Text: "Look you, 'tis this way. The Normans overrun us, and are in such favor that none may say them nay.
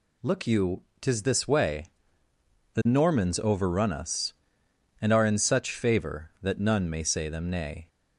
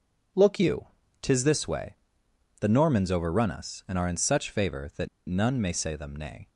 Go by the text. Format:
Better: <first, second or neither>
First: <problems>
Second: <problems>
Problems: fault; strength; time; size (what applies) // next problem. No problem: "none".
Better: first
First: none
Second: pauses between "that" and "none"; slight; at 5.0 s; 0.19 s long